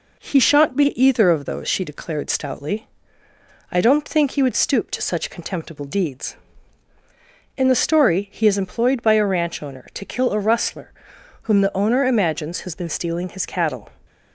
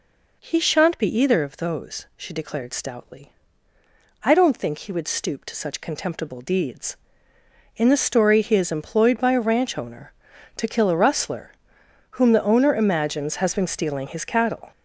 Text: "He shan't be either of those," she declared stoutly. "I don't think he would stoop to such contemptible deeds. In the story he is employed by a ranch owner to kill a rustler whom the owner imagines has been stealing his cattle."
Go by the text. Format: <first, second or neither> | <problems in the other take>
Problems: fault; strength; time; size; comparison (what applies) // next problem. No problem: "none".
first | gets louder; throughout; 6.5 dB // pauses between "rustler" and "whom"; noticeable; at 11.5 s; 0.60 s long; noticeable in the first